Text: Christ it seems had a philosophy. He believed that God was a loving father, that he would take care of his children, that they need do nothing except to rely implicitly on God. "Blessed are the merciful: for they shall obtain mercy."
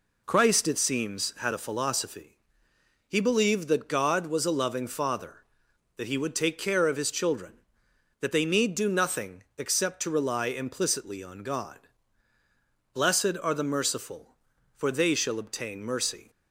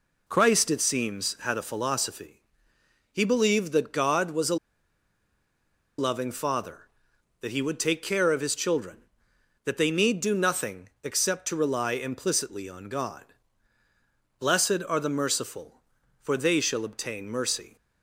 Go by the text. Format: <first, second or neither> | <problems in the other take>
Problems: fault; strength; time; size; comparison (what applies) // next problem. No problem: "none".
first | pauses between "a" and "loving"; strong; at 4.5 s; 1.4 s long // pauses between "nothing" and "except"; slight; at 10.8 s; 0.16 s long; slight in the first